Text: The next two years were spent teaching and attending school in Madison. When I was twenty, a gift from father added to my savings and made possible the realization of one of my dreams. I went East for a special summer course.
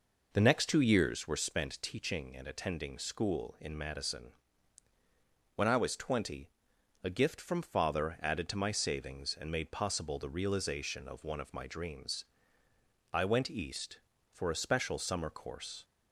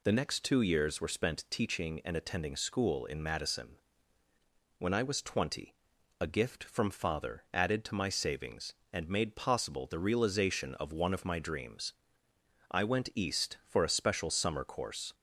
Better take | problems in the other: second | starts louder than the rest; noticeable; until 1.5 s; 5 dB

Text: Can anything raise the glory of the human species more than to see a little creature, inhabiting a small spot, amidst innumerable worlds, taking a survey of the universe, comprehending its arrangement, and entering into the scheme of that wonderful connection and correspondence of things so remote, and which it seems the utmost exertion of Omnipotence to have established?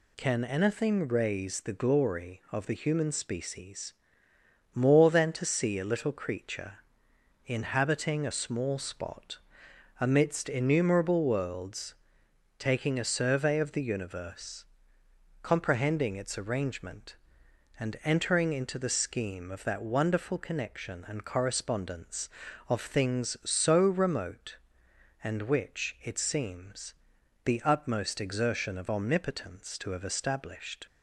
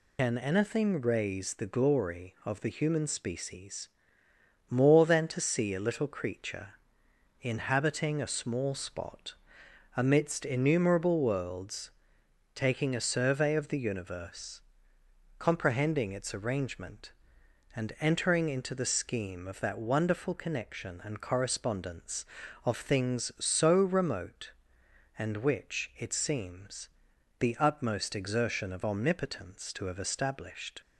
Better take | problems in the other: first | loses the start of "Can"; at 0.1 s; 95 ms // pauses between "species" and "more"; noticeable; at 3.8 s; 0.82 s long; noticeable in the first // pauses between "seems" and "the"; noticeable; at 26.8 s; 0.50 s long; noticeable in the first

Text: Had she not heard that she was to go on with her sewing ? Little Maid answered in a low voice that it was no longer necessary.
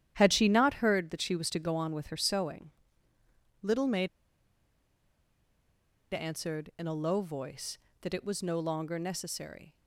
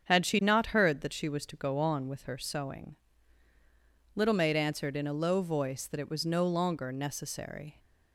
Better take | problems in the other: second | starts louder than the rest; strong; until 1.1 s; 11 dB; strong in the second // pauses between "Maid" and "answered"; strong; at 4.0 s; 2.0 s long

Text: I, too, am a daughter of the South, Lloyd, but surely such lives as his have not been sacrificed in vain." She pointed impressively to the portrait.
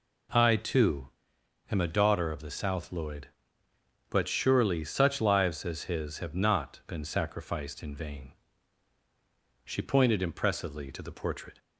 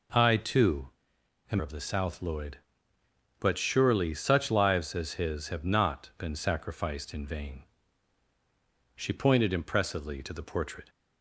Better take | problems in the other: first | skips "a daughter"; at 1.6 s

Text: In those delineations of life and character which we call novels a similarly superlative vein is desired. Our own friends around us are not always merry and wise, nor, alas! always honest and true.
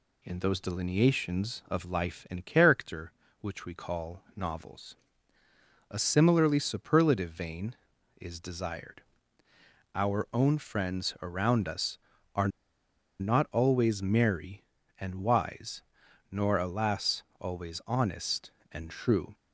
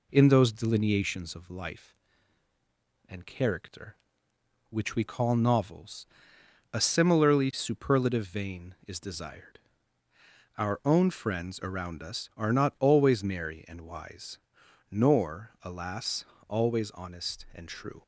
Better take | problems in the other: second | pauses between "novels" and "a"; noticeable; at 4.9 s; 0.96 s long; noticeable in the second // pauses between "are" and "not"; noticeable; at 12.4 s; 0.71 s long

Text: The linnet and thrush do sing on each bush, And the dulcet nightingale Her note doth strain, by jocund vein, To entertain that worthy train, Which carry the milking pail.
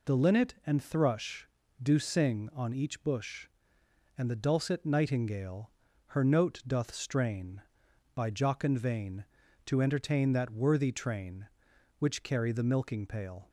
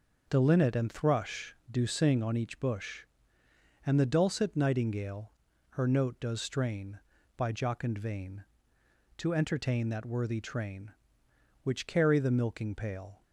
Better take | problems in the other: first | starts louder than the rest; noticeable; until 1.3 s; 6 dB // pauses between "nightingale" and "Her"; at 5.3 s; 0.38 s long; slight in the first // says "does" for "doth"; at 6.1 s

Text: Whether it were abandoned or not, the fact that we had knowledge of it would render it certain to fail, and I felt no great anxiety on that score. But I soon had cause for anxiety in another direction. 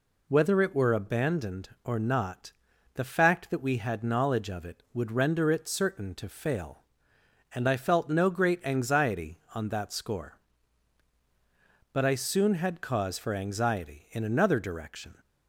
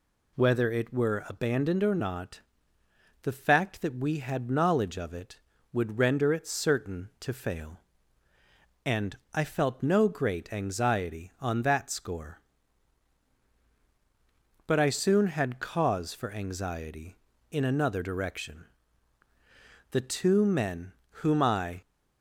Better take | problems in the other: first | pauses between "and" and "I"; slight; at 9.1 s; 0.18 s long // goes on to say "The two men whom I"; strong; from 19.9 s on; 1.9 s long

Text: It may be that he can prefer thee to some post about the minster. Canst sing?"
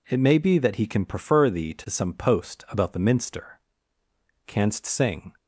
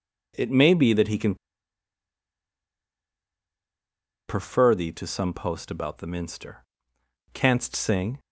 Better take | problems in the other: first | pauses between "can" and "prefer"; strong; at 1.3 s; 2.9 s long

